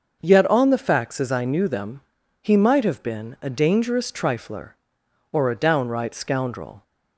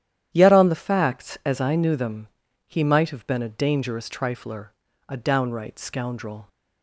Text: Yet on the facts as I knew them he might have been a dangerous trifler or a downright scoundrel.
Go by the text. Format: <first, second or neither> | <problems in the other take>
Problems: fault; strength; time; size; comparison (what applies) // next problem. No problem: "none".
first | starts louder than the rest; strong; until 1.3 s; 11 dB; noticeable in the first // pauses between "them" and "he"; at 2.2 s; 0.38 s long; also in the first // skips "or"; at 4.8 s